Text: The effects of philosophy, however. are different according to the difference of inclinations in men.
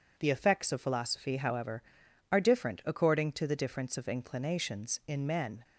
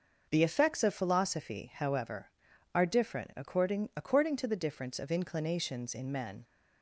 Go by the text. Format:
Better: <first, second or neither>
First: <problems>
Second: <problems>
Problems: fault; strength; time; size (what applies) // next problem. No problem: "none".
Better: first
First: none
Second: says "according" twice; at 3.9 s